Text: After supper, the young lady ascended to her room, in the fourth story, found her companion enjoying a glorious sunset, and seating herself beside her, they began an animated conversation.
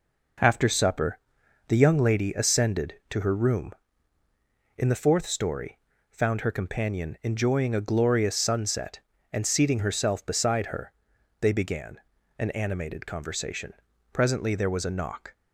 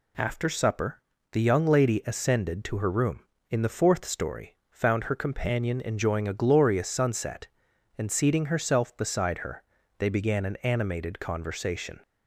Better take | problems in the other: second | pauses between "began" and "an"; at 11.9 s; 0.40 s long // goes on to say "Presently there was a knock"; noticeable; from 14.1 s on; 1.2 s long

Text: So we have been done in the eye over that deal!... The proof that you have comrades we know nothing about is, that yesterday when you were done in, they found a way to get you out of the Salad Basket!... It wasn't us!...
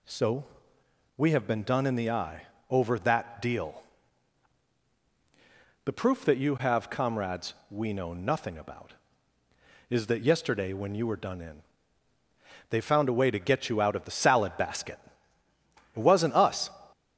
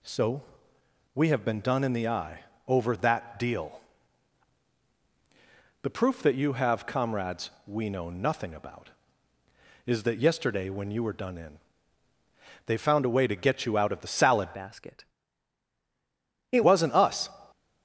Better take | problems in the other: first | pauses between "So" and "we"; noticeable; at 0.4 s; 0.72 s long; noticeable in the first // pauses between "eye" and "over"; slight; at 2.4 s; 0.26 s long; slight in the first // pauses between "comrades" and "we"; slight; at 7.5 s; 0.16 s long; slight in the first // changes voice from "Basket" to "It"; from 14.5 to 16.6 s; 2.1 s long

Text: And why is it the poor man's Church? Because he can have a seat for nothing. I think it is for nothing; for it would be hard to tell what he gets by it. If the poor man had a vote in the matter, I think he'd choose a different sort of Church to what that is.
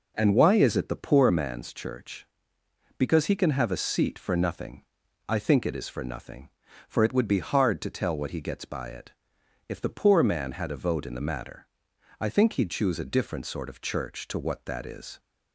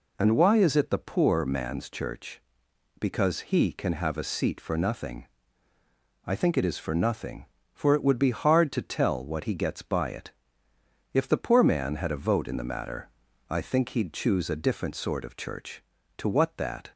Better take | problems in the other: first | stops before "is"; at 16.9 s

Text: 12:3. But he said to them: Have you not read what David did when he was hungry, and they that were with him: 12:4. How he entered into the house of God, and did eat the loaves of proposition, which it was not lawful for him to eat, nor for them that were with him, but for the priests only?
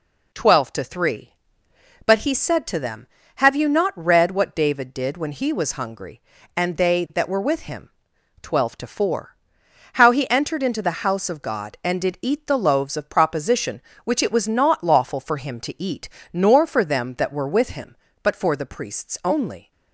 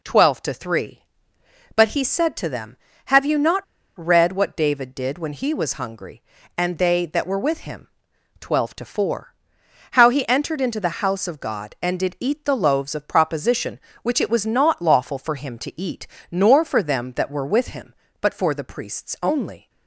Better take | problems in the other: first | pauses between "not" and "read"; slight; at 3.6 s; 0.35 s long

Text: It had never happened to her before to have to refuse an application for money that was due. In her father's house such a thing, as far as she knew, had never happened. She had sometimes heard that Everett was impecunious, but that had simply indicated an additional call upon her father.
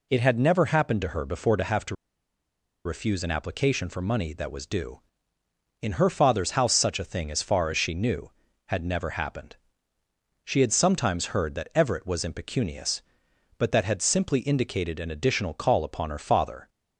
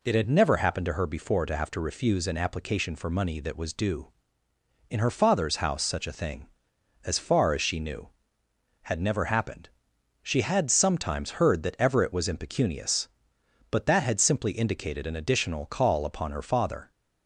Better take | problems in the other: second | pauses between "to" and "refuse"; noticeable; at 1.9 s; 0.90 s long

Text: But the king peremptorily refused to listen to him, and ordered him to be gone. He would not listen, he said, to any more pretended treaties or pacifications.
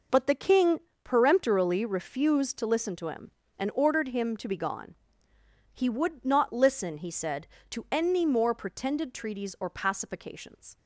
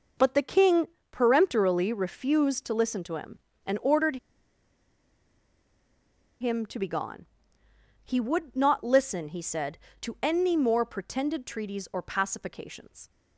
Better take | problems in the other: first | pauses between "king" and "peremptorily"; slight; at 0.8 s; 0.26 s long; slight in the first // pauses between "ordered" and "him"; strong; at 4.1 s; 2.2 s long

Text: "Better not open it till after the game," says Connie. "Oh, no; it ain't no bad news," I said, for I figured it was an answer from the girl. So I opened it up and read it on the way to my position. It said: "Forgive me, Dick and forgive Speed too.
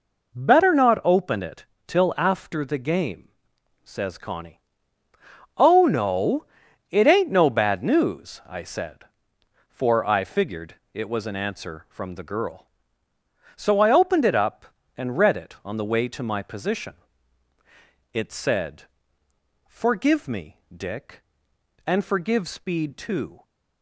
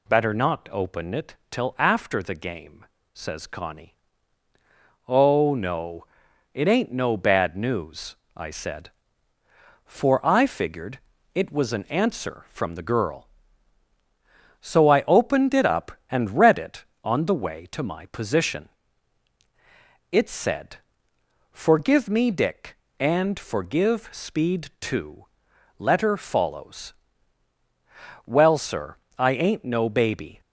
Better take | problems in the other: first | pauses between "it" and "till"; slight; at 1.3 s; 0.16 s long; slight in the first // pauses between "figured" and "it"; slight; at 10.9 s; 0.34 s long; slight in the first // goes on to say "Letter follows Well sir I ain't no baby"; strong; from 25.7 s on; 4.6 s long

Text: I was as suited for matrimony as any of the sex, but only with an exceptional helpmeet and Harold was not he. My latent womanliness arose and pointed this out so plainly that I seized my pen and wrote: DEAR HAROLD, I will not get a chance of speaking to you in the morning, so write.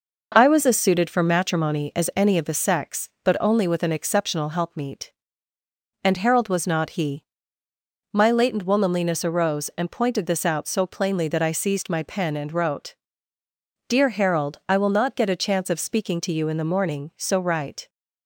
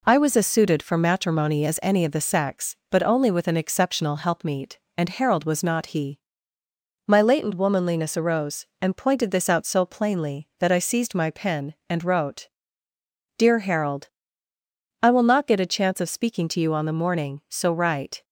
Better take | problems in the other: first | says "on" for "in"; at 16.7 s

